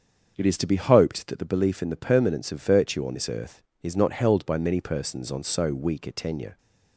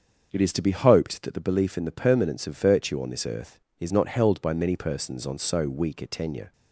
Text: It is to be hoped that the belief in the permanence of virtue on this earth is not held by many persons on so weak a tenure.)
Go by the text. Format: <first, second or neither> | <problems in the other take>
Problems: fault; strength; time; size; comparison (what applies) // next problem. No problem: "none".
neither | starts louder than the rest; the same in both